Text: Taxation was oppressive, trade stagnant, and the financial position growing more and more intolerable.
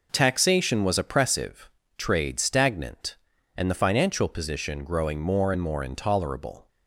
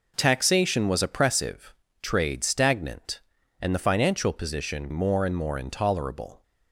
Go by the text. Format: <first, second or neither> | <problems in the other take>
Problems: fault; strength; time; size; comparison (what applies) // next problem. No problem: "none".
first | skips "growing"; at 4.9 s